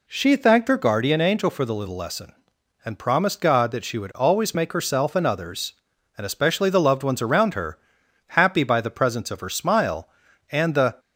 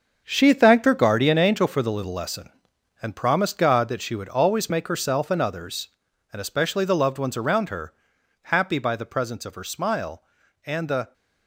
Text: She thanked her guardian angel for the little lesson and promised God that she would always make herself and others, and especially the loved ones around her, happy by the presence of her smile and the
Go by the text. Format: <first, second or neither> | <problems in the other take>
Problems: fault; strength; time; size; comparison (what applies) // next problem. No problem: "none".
first | gets quieter; strong; throughout; 10 dB